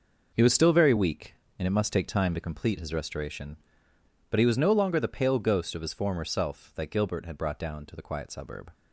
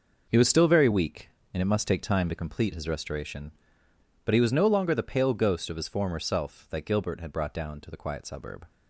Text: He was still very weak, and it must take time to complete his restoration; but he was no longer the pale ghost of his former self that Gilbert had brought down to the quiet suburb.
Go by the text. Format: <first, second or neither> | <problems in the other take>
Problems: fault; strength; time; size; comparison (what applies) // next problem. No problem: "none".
neither | none